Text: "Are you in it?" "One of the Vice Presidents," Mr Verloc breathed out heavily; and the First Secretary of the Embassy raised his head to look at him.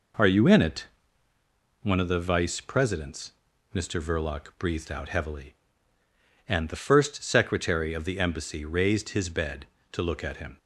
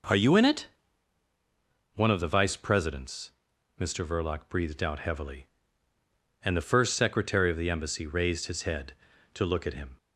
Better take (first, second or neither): second